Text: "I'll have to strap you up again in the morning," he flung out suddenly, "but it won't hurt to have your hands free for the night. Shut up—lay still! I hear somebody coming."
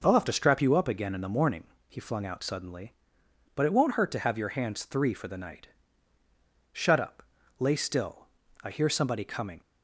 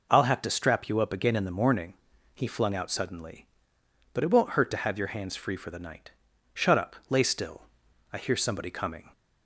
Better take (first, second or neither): second